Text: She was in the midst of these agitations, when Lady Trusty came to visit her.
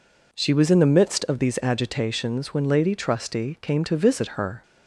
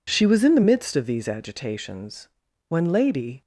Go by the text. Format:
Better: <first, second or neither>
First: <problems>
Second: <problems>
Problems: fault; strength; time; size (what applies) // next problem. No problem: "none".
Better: first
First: none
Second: stops before "Trusty came to visit her"; at 3.4 s